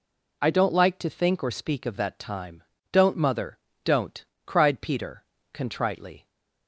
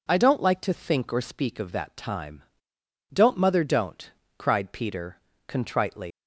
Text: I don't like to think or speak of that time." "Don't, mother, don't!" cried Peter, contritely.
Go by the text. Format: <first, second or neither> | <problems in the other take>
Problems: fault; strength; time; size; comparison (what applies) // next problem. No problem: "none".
first | leaves "contritely" unfinished; at 6.1 s; 120 ms